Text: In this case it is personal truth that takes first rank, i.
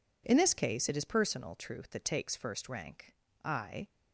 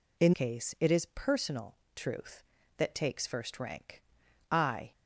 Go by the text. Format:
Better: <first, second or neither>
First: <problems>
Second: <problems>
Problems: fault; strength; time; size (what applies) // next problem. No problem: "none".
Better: first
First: none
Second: skips "this"; at 0.3 s // pauses between "personal" and "truth"; slight; at 1.7 s; 0.20 s long